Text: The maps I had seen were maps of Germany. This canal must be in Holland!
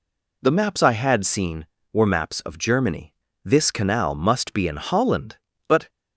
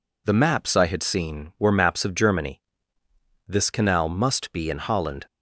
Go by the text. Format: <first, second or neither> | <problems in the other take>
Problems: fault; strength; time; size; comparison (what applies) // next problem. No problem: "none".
second | goes on to say "But"; slight; from 5.6 s on; 0.22 s long